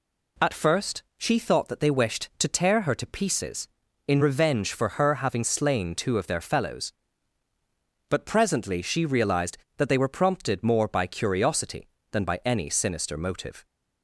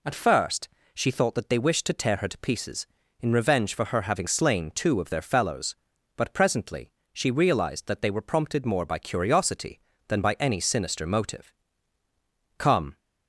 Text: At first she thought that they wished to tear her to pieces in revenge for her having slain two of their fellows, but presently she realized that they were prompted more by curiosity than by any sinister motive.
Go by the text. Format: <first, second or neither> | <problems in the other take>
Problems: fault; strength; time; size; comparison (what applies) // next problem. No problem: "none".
first | pauses between "first" and "she"; slight; at 0.6 s; 0.26 s long // pauses between "presently" and "she"; slight; at 6.9 s; 0.22 s long // goes on to say "Come"; slight; from 12.5 s on; 0.40 s long